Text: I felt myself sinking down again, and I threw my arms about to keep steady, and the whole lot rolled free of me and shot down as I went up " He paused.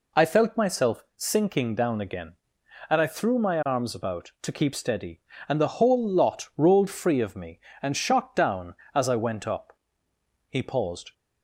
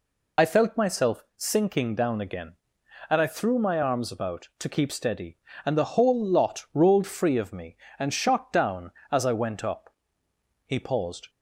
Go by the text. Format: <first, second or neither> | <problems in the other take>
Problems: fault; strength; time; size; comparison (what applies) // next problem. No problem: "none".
first | loses the start of "I"; at 0.3 s; 30 ms